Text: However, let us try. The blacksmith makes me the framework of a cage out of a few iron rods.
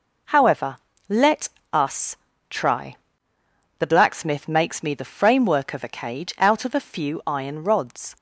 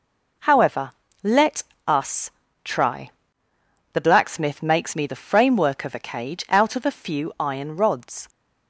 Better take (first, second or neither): neither